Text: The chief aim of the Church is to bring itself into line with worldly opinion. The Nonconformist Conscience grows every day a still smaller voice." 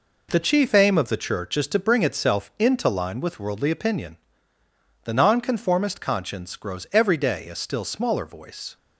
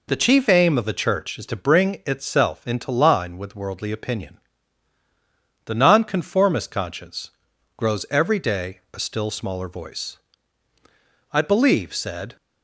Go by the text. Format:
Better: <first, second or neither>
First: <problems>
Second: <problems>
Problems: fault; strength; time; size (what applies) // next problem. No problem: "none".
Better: first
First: none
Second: pauses between "Conscience" and "grows"; at 7.3 s; 0.44 s long // goes on to say "I believe said"; noticeable; from 11.3 s on; 1.0 s long